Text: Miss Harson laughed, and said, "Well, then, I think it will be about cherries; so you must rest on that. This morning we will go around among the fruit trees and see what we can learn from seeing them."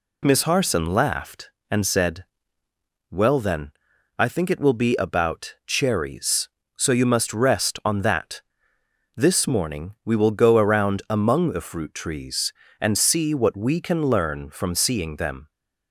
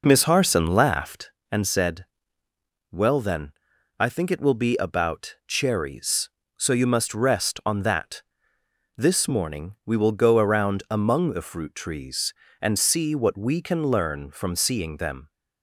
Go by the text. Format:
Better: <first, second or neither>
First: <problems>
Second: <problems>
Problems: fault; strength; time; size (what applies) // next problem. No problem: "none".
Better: first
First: none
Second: starts louder than the rest; noticeable; until 1.4 s; 4.5 dB